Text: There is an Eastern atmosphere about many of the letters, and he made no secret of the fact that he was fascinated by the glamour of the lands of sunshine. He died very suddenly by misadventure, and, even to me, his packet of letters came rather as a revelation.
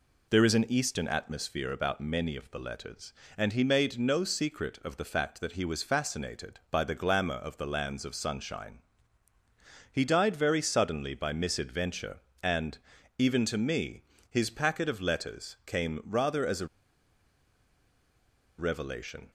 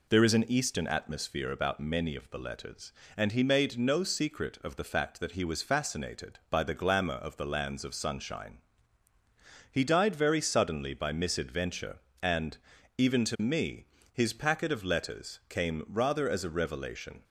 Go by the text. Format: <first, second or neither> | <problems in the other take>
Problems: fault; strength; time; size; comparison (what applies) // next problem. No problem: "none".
second | pauses between "a" and "revelation"; strong; at 16.6 s; 1.9 s long